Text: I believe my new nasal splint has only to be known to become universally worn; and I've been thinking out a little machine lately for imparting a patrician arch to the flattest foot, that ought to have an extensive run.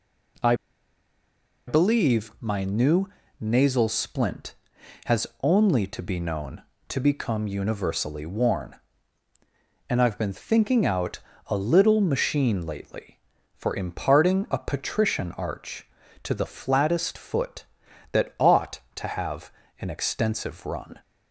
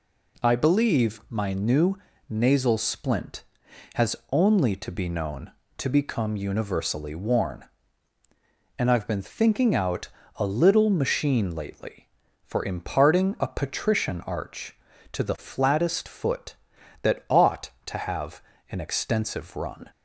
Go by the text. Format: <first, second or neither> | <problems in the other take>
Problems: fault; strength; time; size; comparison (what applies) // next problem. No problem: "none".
second | pauses between "I" and "believe"; at 0.5 s; 1.1 s long // pauses between "new" and "nasal"; slight; at 3.0 s; 0.32 s long; slight in the second // pauses between "out" and "a"; slight; at 11.1 s; 0.28 s long; slight in the second // pauses between "have" and "an"; slight; at 19.5 s; 0.26 s long; slight in the second